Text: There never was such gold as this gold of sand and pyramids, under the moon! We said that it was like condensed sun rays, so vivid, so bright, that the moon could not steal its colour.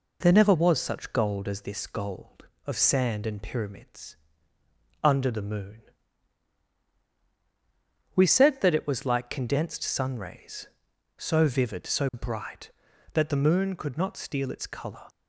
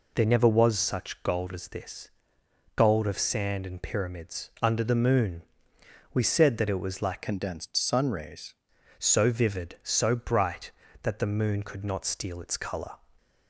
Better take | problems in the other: first | pauses between "this" and "gold"; noticeable; at 2.1 s; 0.64 s long // changes voice from "condensed" to "rays"; from 7.2 to 8.5 s; 1.3 s long

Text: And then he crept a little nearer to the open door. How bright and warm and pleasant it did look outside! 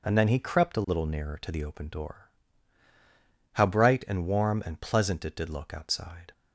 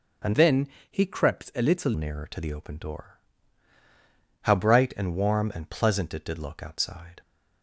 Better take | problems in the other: first | starts louder than the rest; until 1.4 s; 6 dB // changes voice from "then" to "little"; from 0.3 to 1.9 s; 1.6 s long // pauses between "then" and "he"; slight; at 0.6 s; 0.24 s long

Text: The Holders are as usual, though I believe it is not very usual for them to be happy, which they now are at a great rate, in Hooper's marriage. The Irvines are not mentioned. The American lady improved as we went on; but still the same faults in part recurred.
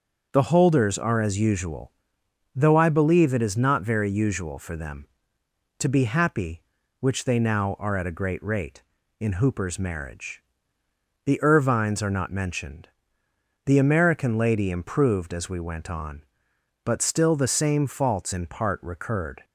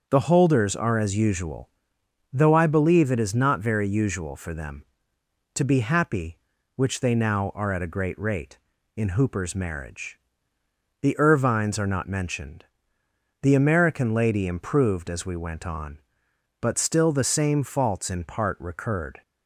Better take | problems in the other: neither | starts louder than the rest; the same in both

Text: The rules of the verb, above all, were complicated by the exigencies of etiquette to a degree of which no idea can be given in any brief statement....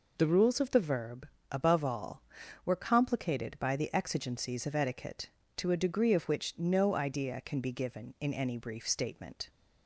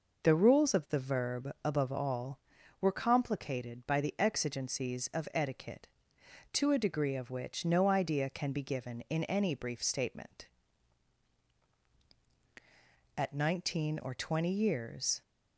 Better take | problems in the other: first | goes on to say "At nineteen or twenty years"; strong; from 13.1 s on; 2.0 s long

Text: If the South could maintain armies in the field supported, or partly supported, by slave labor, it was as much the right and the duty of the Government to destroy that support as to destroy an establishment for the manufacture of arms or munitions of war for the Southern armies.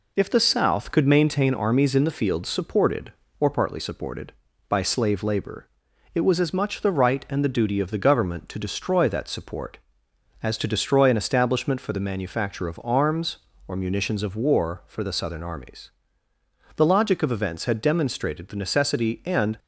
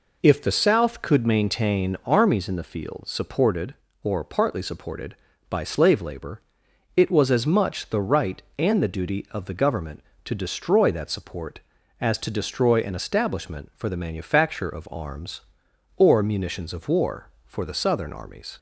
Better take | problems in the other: second | goes on to say "The logic of events had demonstrated the necessity and"; strong; from 16.7 s on; 2.8 s long

